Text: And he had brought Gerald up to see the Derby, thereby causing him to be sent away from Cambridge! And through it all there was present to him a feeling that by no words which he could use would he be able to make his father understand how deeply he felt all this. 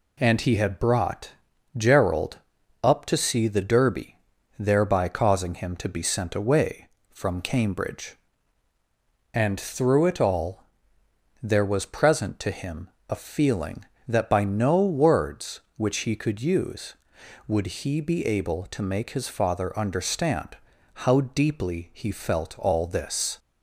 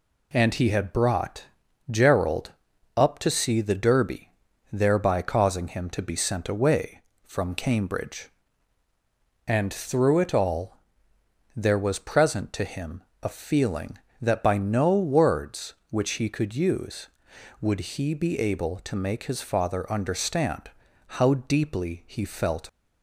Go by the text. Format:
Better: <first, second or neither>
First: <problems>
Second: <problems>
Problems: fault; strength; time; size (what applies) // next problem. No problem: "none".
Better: first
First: pauses between "brought" and "Gerald"; noticeable; at 1.3 s; 0.46 s long // pauses between "Gerald" and "up"; at 2.3 s; 0.44 s long // pauses between "all" and "there"; noticeable; at 10.6 s; 0.76 s long // pauses between "him" and "a"; slight; at 12.8 s; 0.20 s long // pauses between "understand" and "how"; noticeable; at 20.5 s; 0.48 s long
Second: pauses between "brought" and "Gerald"; noticeable; at 1.4 s; 0.46 s long // pauses between "Gerald" and "up"; at 2.5 s; 0.44 s long // pauses between "all" and "there"; noticeable; at 10.7 s; 0.76 s long // pauses between "him" and "a"; slight; at 13.0 s; 0.20 s long // pauses between "understand" and "how"; noticeable; at 20.6 s; 0.48 s long // stops before "all this"; at 22.6 s